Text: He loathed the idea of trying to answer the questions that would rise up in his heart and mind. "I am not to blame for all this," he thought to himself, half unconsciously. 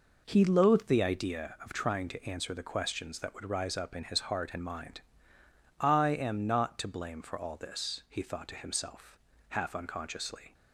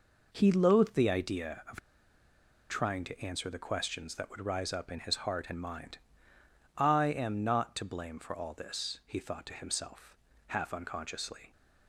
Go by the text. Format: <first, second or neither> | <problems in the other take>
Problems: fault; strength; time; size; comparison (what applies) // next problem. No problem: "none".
first | pauses between "of" and "trying"; noticeable; at 1.7 s; 0.90 s long